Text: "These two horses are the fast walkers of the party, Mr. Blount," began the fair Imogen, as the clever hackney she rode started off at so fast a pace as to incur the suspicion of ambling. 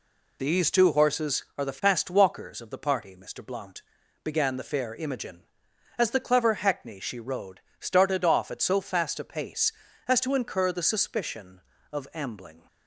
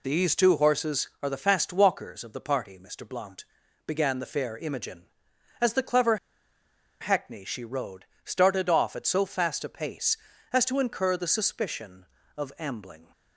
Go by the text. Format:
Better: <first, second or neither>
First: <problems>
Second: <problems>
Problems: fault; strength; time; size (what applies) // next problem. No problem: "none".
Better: first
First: pauses between "rode" and "started"; slight; at 7.6 s; 0.18 s long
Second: pauses between "clever" and "hackney"; noticeable; at 6.1 s; 0.83 s long // pauses between "rode" and "started"; slight; at 8.0 s; 0.18 s long